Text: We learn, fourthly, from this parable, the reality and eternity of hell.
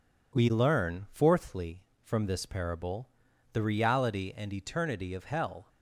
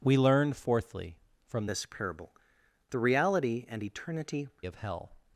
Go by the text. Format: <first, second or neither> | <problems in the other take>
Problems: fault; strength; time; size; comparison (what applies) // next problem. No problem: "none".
first | changes voice from "this" to "eternity"; from 1.6 to 4.4 s; 2.8 s long